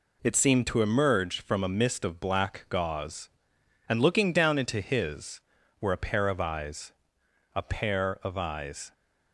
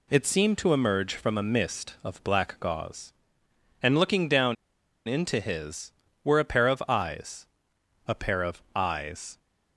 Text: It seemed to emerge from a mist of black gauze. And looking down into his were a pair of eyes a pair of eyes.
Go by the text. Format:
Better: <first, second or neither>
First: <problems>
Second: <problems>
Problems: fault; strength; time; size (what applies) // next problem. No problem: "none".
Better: first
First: pauses between "eyes" and "a"; noticeable; at 6.9 s; 0.62 s long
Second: pauses between "down" and "into"; noticeable; at 4.5 s; 0.51 s long // pauses between "eyes" and "a"; noticeable; at 7.4 s; 0.62 s long